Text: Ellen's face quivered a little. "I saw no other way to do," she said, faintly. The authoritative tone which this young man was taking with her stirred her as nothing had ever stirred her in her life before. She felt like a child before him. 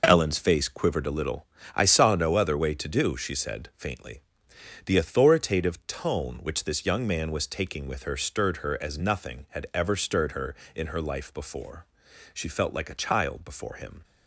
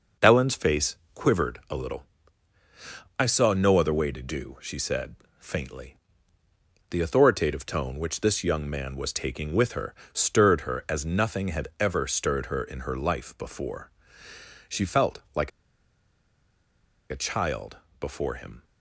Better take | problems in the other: first | pauses between "face" and "quivered"; slight; at 0.9 s; 0.18 s long // pauses between "her" and "stirred"; slight; at 9.9 s; 0.18 s long // pauses between "like" and "a"; strong; at 15.5 s; 1.6 s long // pauses between "child" and "before"; slight; at 17.7 s; 0.24 s long

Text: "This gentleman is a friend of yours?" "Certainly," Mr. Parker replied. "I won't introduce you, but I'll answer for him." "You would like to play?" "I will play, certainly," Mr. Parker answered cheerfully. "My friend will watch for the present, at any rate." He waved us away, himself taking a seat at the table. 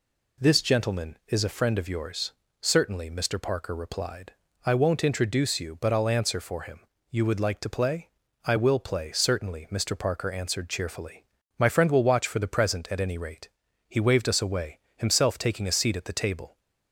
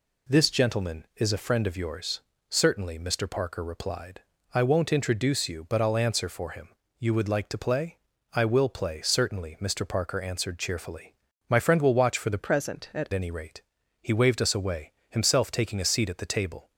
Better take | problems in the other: first | changes voice from "present" to "at"; from 12.3 to 13.0 s; 0.7 s long

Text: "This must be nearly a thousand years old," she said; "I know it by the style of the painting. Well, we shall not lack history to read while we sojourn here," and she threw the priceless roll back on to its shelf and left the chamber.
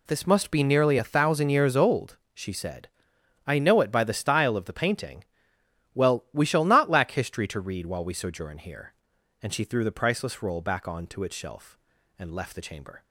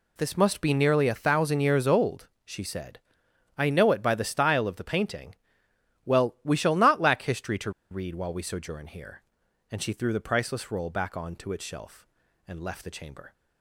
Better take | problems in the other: first | pauses between "to" and "read"; slight; at 7.7 s; 0.20 s long

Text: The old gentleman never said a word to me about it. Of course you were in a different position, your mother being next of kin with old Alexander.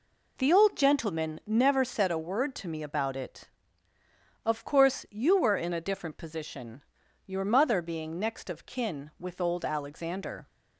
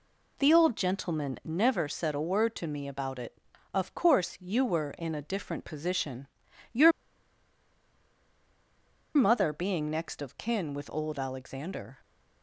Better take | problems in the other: first | pauses between "your" and "mother"; strong; at 6.9 s; 2.2 s long

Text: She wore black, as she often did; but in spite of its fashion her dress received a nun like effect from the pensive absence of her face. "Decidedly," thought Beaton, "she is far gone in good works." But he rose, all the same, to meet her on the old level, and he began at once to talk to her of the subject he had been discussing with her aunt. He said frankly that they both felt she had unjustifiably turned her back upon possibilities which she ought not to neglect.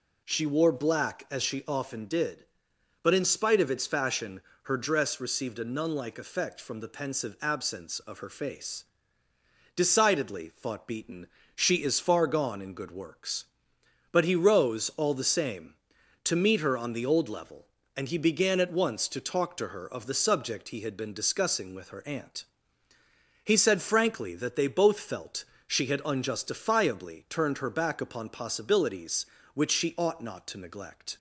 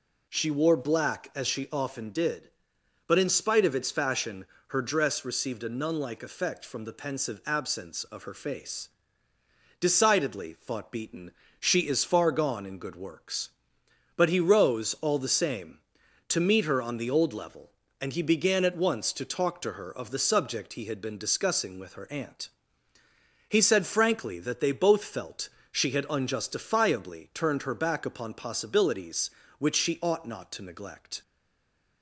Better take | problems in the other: first | pauses between "fashion" and "her"; slight; at 4.4 s; 0.22 s long; slight in the first // pauses between "felt" and "she"; slight; at 25.4 s; 0.20 s long; slight in the first // stays silent after the last word; slight; from 31.2 s on; 0.8 s long

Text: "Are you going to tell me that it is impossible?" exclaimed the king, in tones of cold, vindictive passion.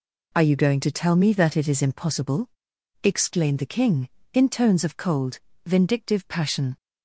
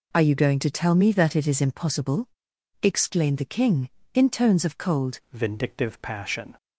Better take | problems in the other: first | changes voice at "vindictive"; from 5.3 s on; 1.2 s long

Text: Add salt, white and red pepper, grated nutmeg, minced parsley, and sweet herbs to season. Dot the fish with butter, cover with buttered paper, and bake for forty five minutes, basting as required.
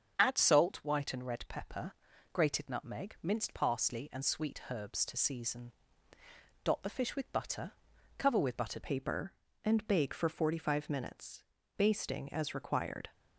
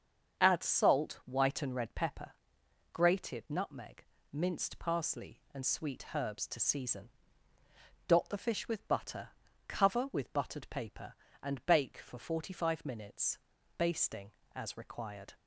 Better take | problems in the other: second | starts louder than the rest; until 1.1 s; 7 dB; also in the second // changes voice at "paper"; from 8.8 s on; 4.2 s long

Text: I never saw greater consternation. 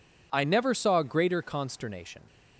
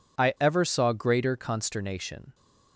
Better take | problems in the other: first | says "ever" for "never"; at 0.3 s

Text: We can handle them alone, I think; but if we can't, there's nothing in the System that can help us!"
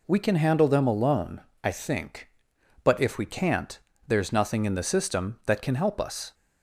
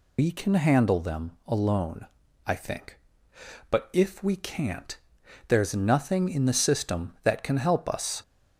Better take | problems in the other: first | loses the start of "We"; at 0.1 s; 130 ms

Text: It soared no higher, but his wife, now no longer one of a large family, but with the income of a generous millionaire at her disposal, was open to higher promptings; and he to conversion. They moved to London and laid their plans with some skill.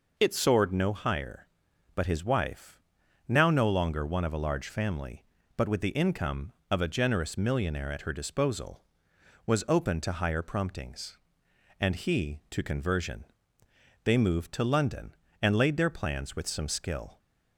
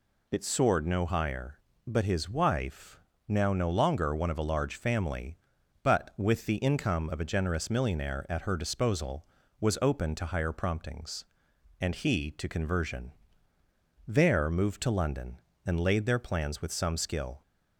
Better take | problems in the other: first | says "There" for "They"; at 14.0 s

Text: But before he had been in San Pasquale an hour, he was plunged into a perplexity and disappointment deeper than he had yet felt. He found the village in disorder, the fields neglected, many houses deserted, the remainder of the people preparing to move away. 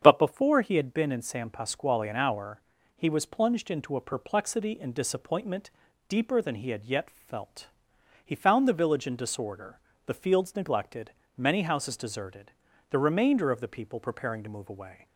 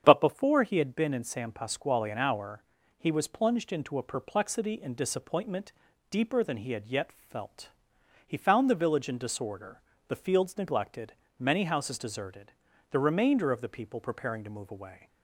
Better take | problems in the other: neither | starts louder than the rest; strong; the same in both // pauses between "disappointment" and "deeper"; the same in both

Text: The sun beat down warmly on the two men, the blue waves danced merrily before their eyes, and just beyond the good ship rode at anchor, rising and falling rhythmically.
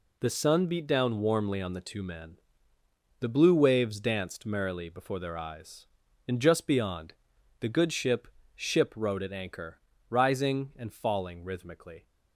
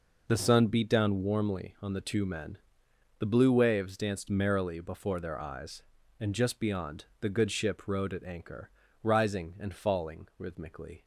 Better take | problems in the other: second | pauses between "beyond" and "the"; noticeable; at 7.1 s; 0.48 s long; slight in the second // says "ship" twice; at 8.5 s

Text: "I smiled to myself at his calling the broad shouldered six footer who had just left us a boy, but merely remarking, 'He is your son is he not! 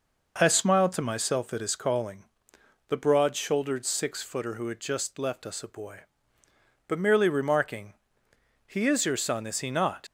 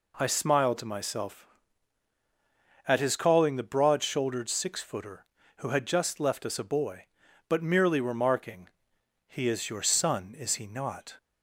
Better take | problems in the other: second | pauses between "calling" and "the"; noticeable; at 2.2 s; 0.64 s long // leaves "not" unfinished; at 10.0 s; 70 ms

